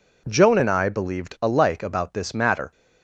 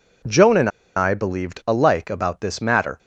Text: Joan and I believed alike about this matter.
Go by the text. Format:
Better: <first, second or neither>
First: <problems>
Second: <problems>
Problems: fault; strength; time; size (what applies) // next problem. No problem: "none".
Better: first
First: none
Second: pauses between "and" and "I"; slight; at 0.7 s; 0.26 s long